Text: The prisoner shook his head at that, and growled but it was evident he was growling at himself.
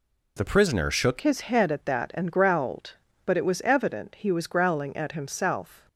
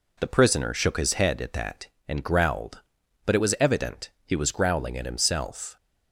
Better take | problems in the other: second | changes voice at "his"; from 1.2 s on; 4.6 s long

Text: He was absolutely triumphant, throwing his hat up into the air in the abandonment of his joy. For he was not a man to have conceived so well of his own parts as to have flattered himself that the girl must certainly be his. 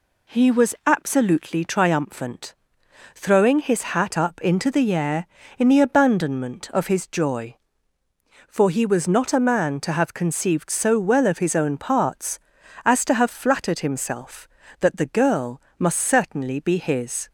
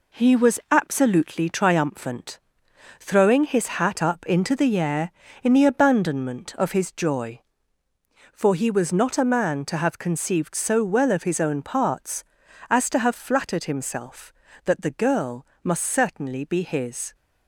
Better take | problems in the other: first | gets quieter; throughout; 6.5 dB // pauses between "girl" and "must"; slight; at 15.4 s; 0.18 s long; slight in the first

